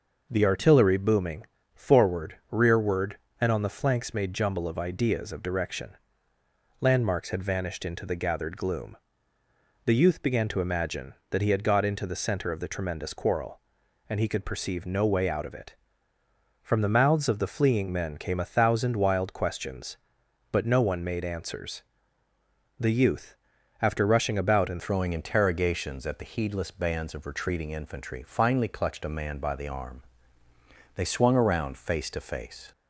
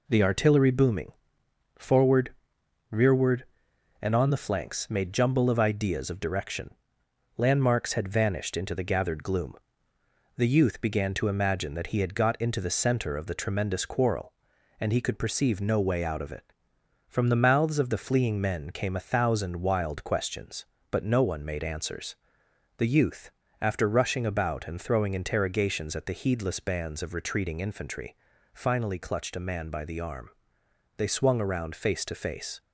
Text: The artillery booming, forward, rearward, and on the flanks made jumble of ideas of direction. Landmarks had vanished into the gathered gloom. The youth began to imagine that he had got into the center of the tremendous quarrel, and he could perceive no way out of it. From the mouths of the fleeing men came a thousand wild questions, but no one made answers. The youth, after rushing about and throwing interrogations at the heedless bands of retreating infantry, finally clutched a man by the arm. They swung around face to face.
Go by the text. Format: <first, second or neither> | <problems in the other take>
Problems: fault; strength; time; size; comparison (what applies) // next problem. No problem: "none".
second | changes voice at "throwing"; from 24.7 s on; 8.0 s long